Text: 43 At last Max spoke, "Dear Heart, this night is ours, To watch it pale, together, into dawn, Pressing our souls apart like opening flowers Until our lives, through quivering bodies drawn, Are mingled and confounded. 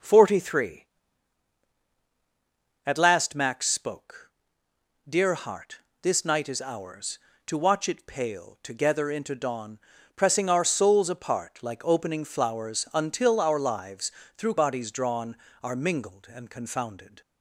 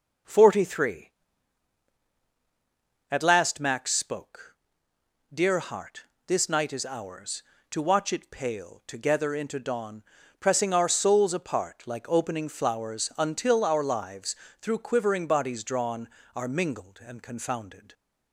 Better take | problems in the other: second | skips "quivering"; at 14.5 s

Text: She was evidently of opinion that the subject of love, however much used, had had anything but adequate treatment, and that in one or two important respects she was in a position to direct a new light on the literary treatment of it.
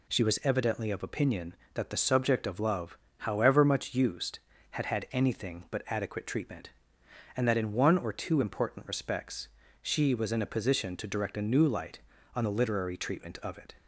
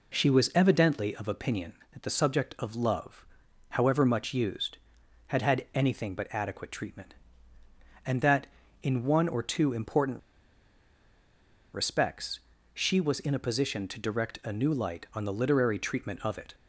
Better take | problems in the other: first | pauses between "important" and "respects"; strong; at 10.1 s; 1.5 s long // pauses between "respects" and "she"; slight; at 12.3 s; 0.34 s long; slight in the first

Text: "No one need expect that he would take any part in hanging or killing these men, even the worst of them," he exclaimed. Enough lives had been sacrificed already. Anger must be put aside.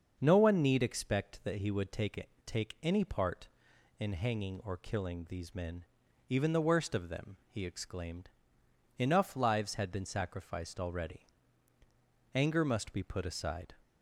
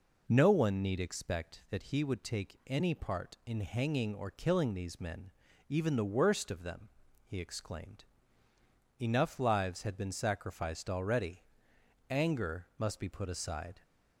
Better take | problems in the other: second | starts louder than the rest; until 1.2 s; 6.5 dB // says "take" twice; at 2.4 s

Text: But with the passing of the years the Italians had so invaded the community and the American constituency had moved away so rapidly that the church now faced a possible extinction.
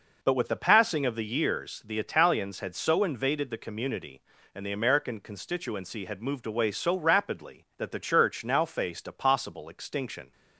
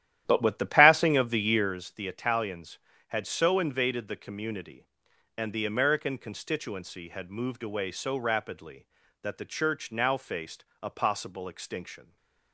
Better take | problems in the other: first | starts louder than the rest; strong; until 1.8 s; 12 dB // pauses between "faced" and "a"; slight; at 10.6 s; 0.18 s long // stays silent after the last word; slight; from 12.0 s on; 0.5 s long

